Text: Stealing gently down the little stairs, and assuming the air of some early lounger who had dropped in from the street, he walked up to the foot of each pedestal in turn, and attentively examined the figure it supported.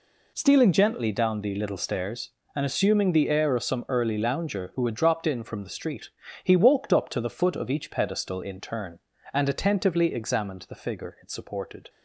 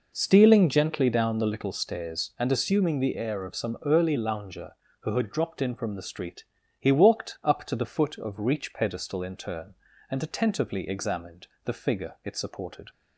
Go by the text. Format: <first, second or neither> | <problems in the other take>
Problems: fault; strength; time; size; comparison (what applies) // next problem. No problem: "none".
first | says "reach" for "each"; at 8.3 s // pauses between "examined" and "the"; slight; at 11.4 s; 0.16 s long